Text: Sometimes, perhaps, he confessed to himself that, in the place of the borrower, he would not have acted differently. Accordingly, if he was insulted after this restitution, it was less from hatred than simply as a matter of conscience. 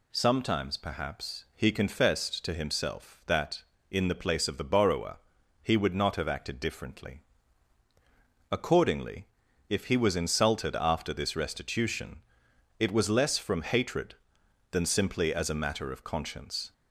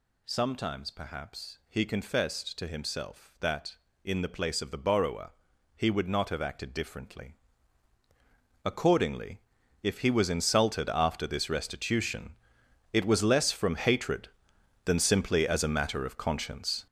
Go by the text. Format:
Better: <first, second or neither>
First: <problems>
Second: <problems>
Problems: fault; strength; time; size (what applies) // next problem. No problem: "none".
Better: first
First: none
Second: gets louder; strong; throughout; 8.5 dB